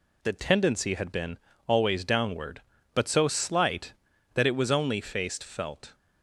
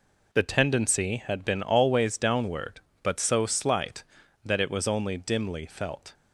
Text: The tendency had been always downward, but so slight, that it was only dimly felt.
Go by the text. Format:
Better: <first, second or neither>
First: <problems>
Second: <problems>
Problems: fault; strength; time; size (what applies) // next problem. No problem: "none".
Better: second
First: pauses between "been" and "always"; slight; at 1.3 s; 0.28 s long // says "faced" for "dimly"; at 5.0 s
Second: none